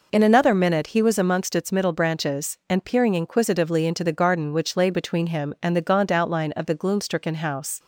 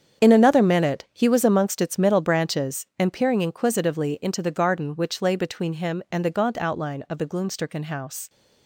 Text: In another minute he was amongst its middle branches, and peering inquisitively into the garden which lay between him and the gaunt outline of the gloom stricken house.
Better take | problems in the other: first | gets quieter; strong; throughout; 11 dB

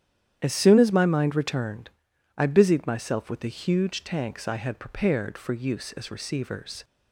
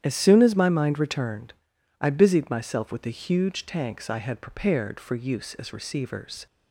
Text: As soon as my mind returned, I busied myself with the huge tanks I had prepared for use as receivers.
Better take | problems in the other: neither | starts louder than the rest; strong; the same in both

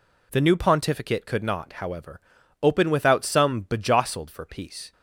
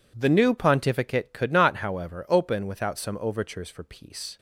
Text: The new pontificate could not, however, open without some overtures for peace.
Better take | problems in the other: second | says "bejostled" for "overtures"; at 3.6 s

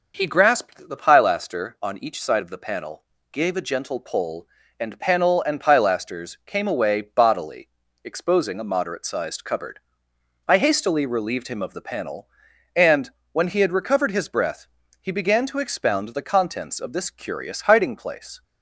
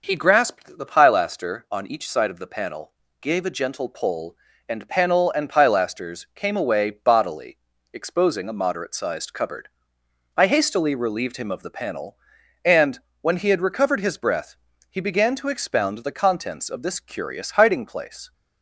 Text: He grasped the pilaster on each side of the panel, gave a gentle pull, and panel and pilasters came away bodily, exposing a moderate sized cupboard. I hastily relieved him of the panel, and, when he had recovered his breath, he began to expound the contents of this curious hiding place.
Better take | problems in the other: neither | none

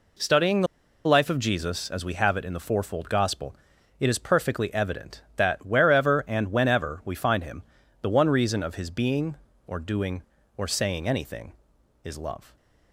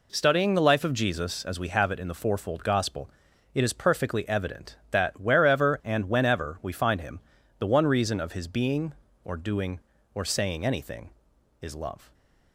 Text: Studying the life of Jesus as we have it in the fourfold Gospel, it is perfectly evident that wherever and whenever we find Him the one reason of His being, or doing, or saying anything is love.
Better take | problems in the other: second | pauses between "the" and "life"; at 0.6 s; 0.39 s long // pauses between "Him" and "the"; at 7.6 s; 0.38 s long; also in the second

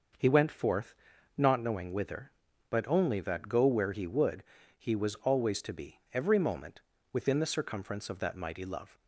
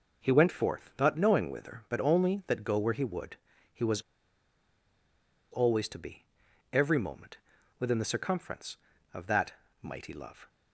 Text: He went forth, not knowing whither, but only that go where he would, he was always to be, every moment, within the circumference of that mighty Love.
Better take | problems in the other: first | pauses between "was" and "always"; strong; at 4.0 s; 1.4 s long // pauses between "that" and "mighty"; slight; at 9.5 s; 0.28 s long

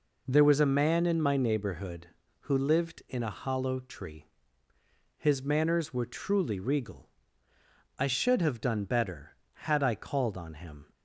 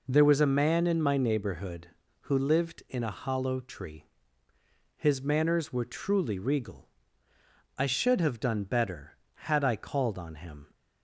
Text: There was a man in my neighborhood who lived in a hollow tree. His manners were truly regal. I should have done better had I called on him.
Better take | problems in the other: neither | none

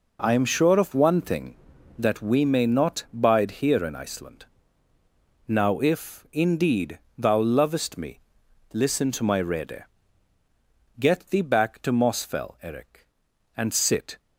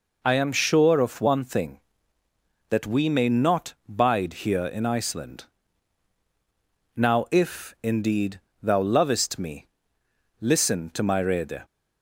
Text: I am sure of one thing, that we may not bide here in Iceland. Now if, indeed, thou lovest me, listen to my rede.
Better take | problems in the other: second | goes on to say "Get thee back to Mosfell Eric and sit"; strong; from 10.9 s on; 3.2 s long

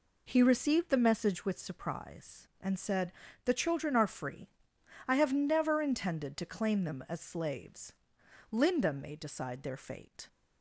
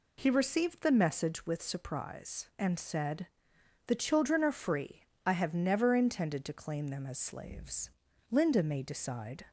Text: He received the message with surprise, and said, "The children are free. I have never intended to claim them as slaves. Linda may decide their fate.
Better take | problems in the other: first | stops before "their fate"; at 9.4 s

